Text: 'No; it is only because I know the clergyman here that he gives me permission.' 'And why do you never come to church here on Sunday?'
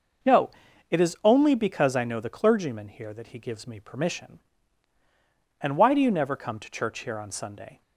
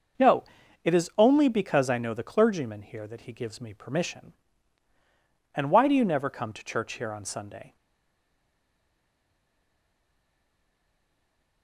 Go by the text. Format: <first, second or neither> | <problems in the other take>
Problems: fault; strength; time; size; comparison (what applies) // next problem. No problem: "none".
first | starts louder than the rest; noticeable; until 1.6 s; 6 dB // stays silent after the last word; strong; from 7.7 s on; 3.9 s long